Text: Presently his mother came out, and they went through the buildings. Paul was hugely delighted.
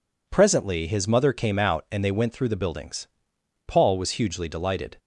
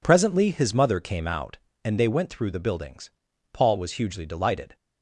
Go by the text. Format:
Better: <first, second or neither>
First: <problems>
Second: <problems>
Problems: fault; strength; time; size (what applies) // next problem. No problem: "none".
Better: neither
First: none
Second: none